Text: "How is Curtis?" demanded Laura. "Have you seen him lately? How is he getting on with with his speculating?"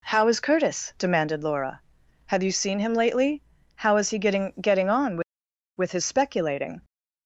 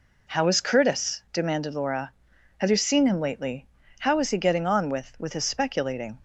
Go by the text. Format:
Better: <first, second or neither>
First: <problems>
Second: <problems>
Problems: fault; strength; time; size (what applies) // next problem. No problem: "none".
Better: second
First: says "getting" twice; at 4.5 s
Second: none